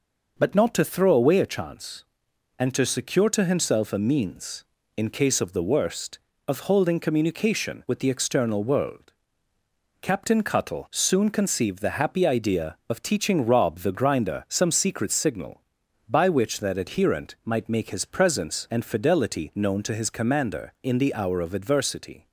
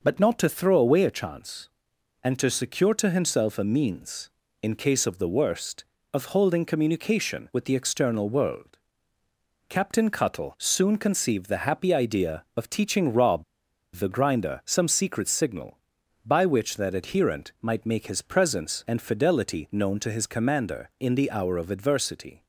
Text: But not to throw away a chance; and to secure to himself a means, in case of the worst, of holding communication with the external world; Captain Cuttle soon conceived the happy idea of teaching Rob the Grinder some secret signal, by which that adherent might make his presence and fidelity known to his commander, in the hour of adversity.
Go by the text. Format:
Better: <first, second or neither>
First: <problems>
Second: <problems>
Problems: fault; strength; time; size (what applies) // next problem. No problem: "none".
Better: first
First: none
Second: pauses between "Rob" and "the"; noticeable; at 13.4 s; 0.51 s long